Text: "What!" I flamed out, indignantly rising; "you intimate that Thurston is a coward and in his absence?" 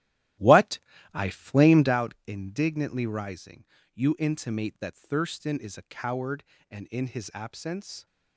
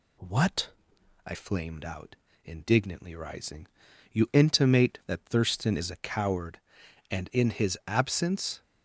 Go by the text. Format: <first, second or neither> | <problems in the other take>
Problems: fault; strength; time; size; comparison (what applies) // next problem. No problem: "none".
second | starts louder than the rest; strong; until 2.0 s; 14 dB